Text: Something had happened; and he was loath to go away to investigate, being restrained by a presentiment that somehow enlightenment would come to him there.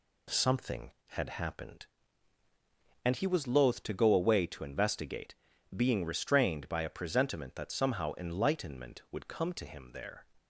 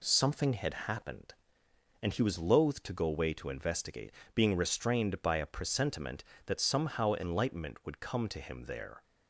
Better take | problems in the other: neither | none

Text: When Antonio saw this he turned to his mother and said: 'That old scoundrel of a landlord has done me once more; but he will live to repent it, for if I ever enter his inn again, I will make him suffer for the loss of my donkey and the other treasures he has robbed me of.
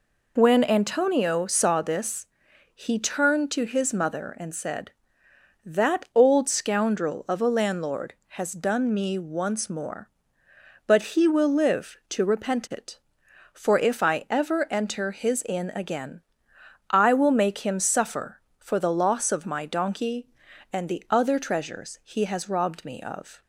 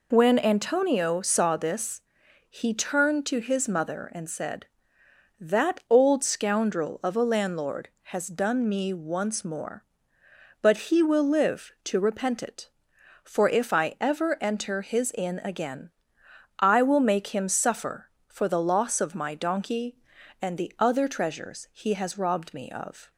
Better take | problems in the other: neither | pauses between "this" and "he"; noticeable; the same in both

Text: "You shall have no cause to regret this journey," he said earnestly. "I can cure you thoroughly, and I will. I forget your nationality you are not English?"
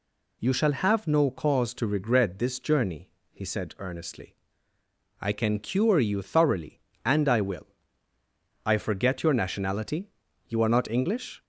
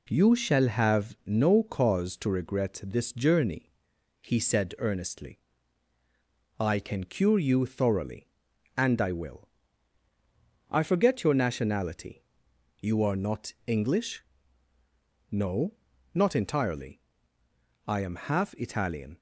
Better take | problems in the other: first | pauses between "nationality" and "you"; noticeable; at 12.2 s; 0.58 s long; also in the first // goes on to say "No not entirely I am half Italian"; strong; from 15.2 s on; 3.8 s long

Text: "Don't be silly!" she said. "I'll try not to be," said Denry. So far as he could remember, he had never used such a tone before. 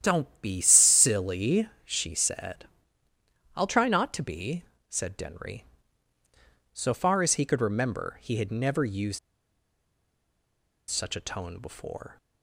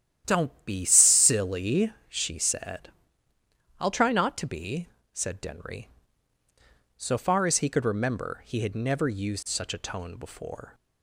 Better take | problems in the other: second | starts louder than the rest; strong; until 1.0 s; 10.5 dB; strong in the second // pauses between "used" and "such"; strong; at 9.1 s; 1.7 s long

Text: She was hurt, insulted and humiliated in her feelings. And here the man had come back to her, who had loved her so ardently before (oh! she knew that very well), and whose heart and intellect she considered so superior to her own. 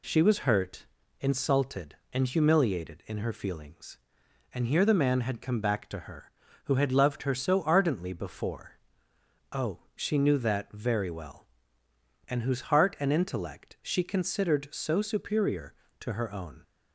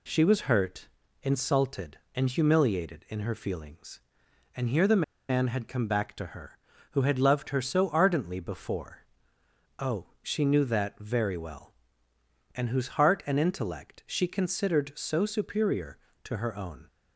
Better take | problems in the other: first | pauses between "the" and "man"; slight; at 5.0 s; 0.26 s long

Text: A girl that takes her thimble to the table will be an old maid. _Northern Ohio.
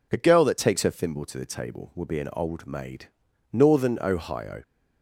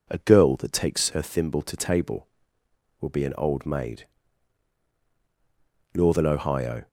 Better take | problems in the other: first | skips "the"; at 1.7 s

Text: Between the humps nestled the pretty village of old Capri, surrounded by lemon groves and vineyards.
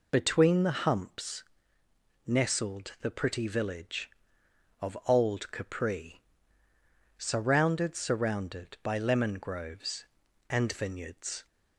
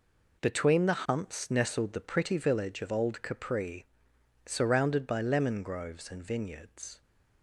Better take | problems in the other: second | pauses between "humps" and "nestled"; noticeable; at 1.4 s; 0.85 s long // says "surrounded" twice; at 7.9 s

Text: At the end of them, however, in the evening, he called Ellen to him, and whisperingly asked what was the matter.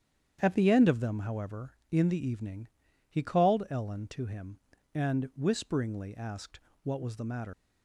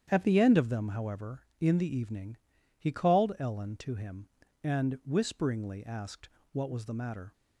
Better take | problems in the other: second | starts louder than the rest; strong; until 1.4 s; 8.5 dB; strong in the second // pauses between "asked" and "what"; slight; at 6.5 s; 0.24 s long; slight in the second // leaves "matter" unfinished; at 7.5 s; 100 ms

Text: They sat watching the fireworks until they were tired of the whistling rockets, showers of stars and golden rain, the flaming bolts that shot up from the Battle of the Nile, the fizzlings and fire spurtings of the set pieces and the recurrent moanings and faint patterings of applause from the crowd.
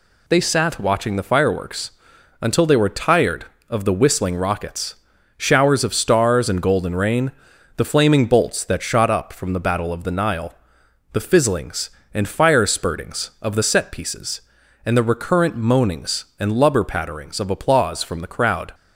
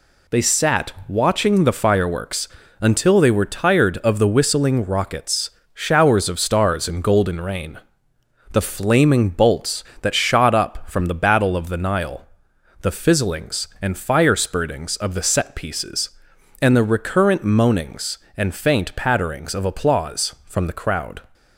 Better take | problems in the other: second | pauses between "fireworks" and "until"; noticeable; at 1.9 s; 0.50 s long; slight in the second // says "lubber" for "faint"; at 16.5 s

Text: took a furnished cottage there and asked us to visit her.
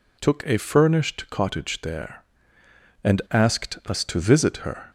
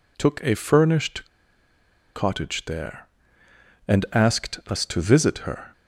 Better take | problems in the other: first | pauses between "furnished" and "cottage"; noticeable; at 1.2 s; 0.88 s long

